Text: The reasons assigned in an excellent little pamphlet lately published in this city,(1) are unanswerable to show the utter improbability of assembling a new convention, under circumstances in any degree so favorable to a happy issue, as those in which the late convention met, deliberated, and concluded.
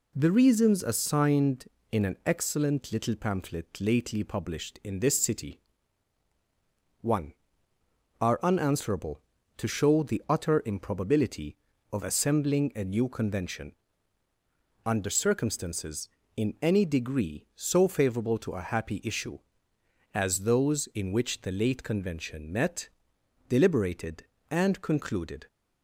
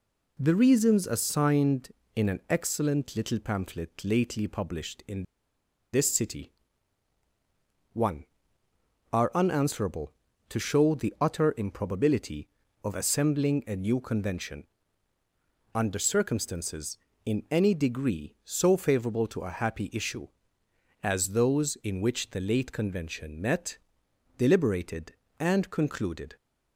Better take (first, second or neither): first